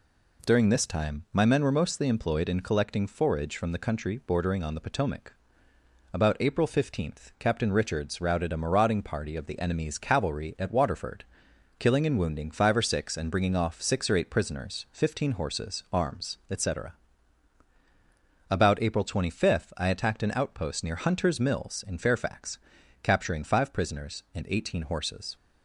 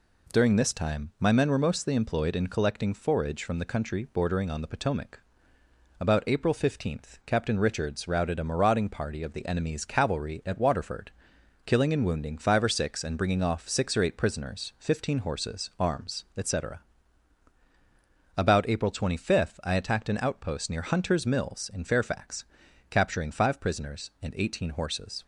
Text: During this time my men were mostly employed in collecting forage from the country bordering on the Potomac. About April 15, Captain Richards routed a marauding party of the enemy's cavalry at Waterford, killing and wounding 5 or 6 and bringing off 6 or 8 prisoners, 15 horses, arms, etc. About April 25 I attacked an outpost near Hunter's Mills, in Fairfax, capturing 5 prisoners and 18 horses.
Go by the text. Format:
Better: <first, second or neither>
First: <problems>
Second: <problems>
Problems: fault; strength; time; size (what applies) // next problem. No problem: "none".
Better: neither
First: none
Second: none